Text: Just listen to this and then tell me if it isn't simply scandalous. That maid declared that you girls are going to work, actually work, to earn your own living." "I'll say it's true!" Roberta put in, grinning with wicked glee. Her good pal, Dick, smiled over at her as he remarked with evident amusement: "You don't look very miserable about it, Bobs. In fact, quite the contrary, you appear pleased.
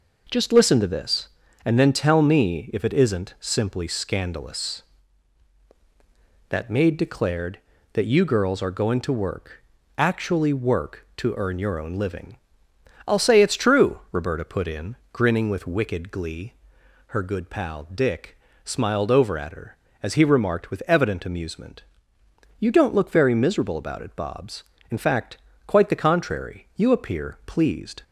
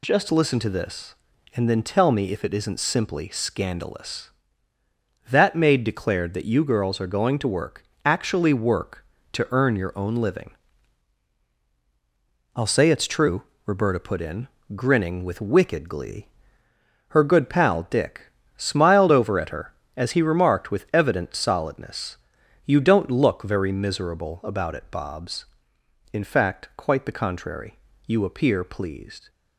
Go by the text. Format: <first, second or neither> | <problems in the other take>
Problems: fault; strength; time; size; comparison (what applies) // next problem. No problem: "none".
first | says "solidness" for "amusement"; at 21.3 s